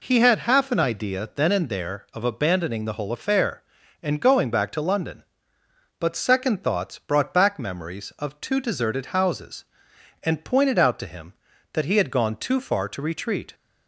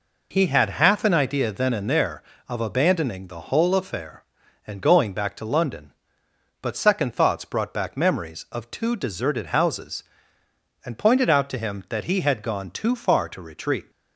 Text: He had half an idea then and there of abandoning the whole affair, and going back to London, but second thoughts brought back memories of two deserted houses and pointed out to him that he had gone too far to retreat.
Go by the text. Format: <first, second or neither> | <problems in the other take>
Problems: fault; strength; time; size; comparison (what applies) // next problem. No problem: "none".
neither | none